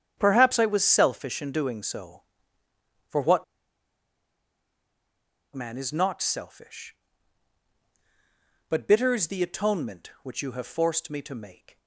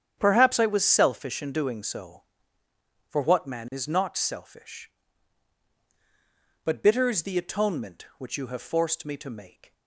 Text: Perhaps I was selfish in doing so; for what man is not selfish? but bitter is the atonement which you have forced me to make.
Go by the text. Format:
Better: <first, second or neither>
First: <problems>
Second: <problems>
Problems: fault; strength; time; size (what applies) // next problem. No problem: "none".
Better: second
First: starts louder than the rest; strong; until 1.1 s; 9 dB // pauses between "what" and "man"; strong; at 3.4 s; 2.1 s long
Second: starts louder than the rest; strong; until 1.1 s; 9 dB